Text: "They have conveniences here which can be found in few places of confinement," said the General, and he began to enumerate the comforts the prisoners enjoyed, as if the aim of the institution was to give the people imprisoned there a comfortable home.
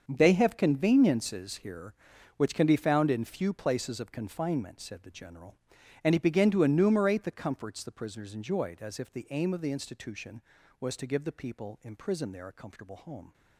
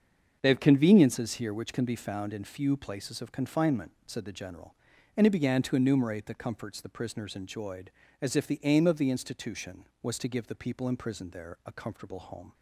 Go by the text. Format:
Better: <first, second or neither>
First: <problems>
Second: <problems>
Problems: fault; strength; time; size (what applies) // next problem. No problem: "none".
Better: second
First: gets quieter; strong; throughout; 13.5 dB // starts louder than the rest; until 1.0 s; 6.5 dB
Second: starts louder than the rest; until 1.4 s; 6.5 dB